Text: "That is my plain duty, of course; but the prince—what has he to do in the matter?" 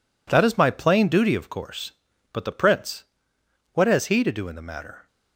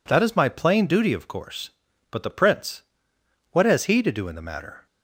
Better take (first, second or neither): second